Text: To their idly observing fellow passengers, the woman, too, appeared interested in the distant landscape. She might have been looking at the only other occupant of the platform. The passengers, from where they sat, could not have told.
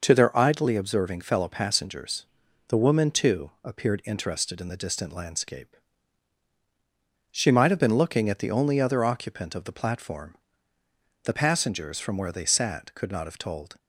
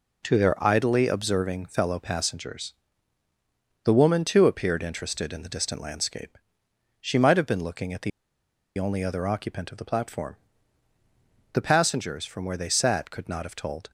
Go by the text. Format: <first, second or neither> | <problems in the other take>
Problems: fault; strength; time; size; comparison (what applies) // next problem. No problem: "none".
first | pauses between "the" and "only"; noticeable; at 8.1 s; 0.68 s long